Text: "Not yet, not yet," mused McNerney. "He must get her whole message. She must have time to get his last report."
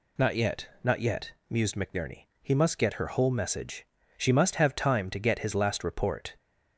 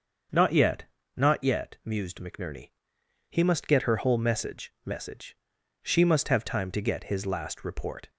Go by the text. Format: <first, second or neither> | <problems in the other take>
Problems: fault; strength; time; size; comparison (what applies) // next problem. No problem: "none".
first | starts louder than the rest; until 1.6 s; 6.5 dB // says "message" twice; at 4.8 s